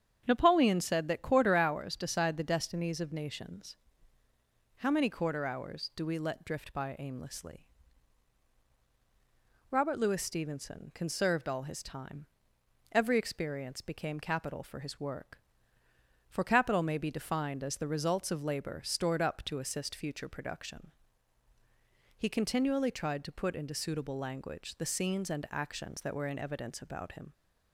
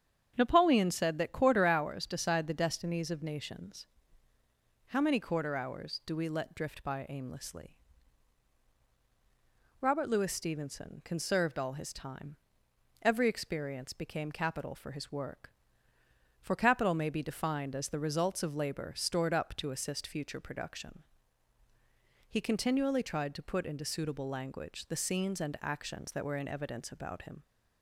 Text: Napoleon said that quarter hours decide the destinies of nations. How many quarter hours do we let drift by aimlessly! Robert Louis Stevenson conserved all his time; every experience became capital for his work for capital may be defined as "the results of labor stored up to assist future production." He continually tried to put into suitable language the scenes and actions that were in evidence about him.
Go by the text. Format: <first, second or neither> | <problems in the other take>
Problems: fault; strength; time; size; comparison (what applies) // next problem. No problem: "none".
neither | starts louder than the rest; strong; the same in both